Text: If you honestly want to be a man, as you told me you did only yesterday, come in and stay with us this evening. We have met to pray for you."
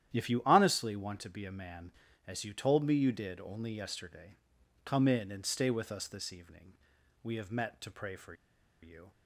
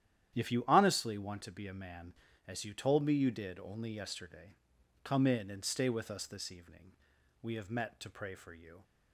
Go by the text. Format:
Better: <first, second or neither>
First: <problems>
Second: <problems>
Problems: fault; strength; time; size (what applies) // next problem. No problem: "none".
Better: second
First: starts louder than the rest; strong; until 1.1 s; 10.5 dB // pauses between "for" and "you"; noticeable; at 8.3 s; 0.48 s long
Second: starts louder than the rest; strong; until 1.3 s; 10.5 dB